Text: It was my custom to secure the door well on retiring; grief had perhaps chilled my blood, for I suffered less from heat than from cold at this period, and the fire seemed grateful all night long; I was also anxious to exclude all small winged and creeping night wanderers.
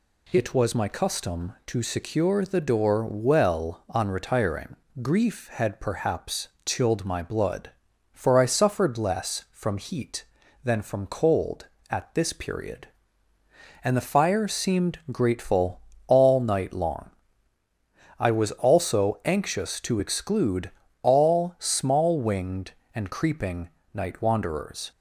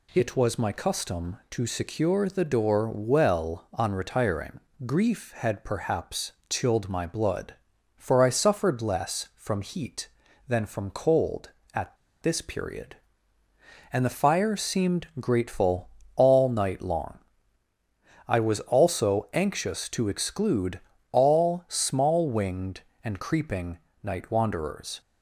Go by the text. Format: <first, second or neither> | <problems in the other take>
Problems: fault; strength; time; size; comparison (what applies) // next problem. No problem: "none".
first | pauses between "perhaps" and "chilled"; slight; at 6.3 s; 0.18 s long; slight in the first // pauses between "at" and "this"; slight; at 11.9 s; 0.28 s long // pauses between "grateful" and "all"; slight; at 15.8 s; 0.28 s long; slight in the first // pauses between "exclude" and "all"; slight; at 20.8 s; 0.32 s long; slight in the first // pauses between "creeping" and "night"; slight; at 23.7 s; 0.24 s long; slight in the first